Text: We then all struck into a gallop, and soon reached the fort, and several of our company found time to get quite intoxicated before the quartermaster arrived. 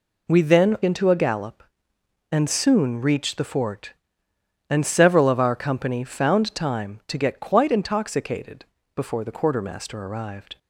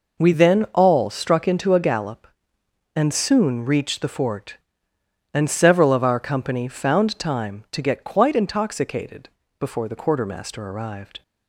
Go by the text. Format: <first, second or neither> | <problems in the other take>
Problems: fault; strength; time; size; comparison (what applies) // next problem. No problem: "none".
second | skips "all struck"; at 0.8 s // pauses between "intoxicated" and "before"; slight; at 8.6 s; 0.28 s long; slight in the second